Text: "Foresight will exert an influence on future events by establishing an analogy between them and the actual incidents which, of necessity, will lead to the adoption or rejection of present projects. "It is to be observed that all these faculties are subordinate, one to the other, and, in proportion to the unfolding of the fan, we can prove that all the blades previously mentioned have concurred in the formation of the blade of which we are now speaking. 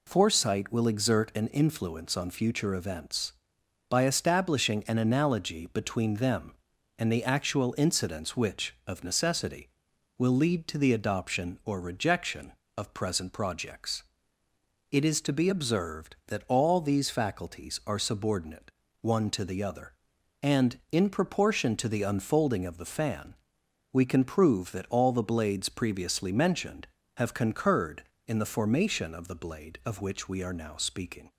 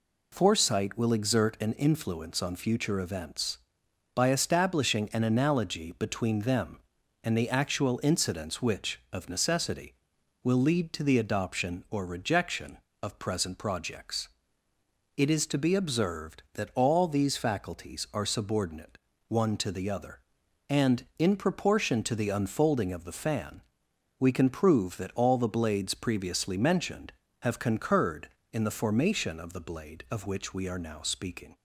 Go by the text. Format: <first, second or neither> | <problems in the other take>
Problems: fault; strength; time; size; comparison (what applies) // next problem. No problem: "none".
neither | none